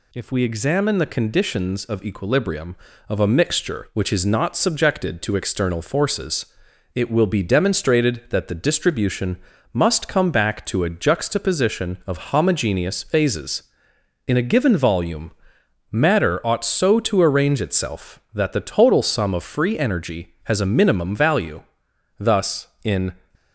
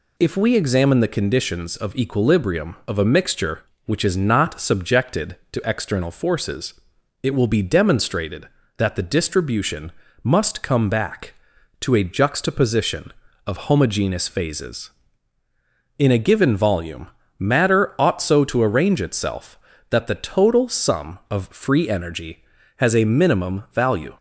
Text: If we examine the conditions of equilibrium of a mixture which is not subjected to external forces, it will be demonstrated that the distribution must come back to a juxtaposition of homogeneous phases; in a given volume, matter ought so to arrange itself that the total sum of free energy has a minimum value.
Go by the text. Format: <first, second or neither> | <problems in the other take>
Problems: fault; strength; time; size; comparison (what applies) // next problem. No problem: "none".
second | pauses between "distribution" and "must"; slight; at 9.3 s; 0.34 s long; slight in the second // goes on to say "Thus in"; noticeable; from 22.1 s on; 0.94 s long